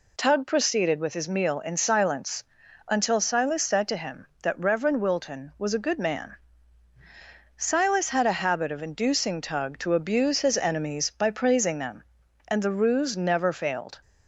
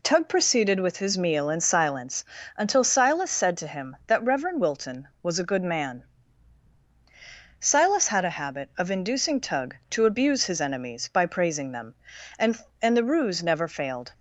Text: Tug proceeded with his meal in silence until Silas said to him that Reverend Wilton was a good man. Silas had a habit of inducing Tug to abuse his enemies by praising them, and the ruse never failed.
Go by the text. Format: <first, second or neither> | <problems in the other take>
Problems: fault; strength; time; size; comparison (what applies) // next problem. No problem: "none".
first | pauses between "silence" and "until"; slight; at 2.2 s; 0.32 s long; also in the first // says "and" twice; at 12.8 s